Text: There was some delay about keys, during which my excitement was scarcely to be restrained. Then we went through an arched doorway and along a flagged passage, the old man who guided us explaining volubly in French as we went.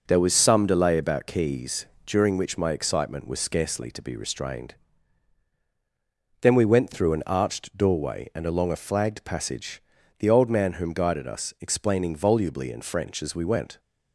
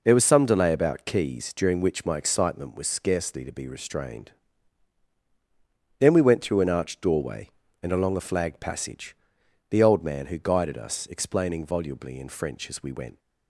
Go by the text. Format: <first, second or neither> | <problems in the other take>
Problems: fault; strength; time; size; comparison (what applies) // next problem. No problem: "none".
second | says "whom" for "who"; at 10.7 s